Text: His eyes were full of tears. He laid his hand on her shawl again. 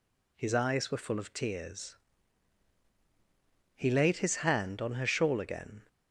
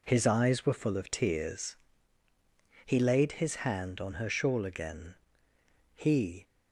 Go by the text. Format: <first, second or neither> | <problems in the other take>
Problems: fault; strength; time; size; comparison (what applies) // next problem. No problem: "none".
first | goes on to say "He"; slight; from 5.9 s on; 0.48 s long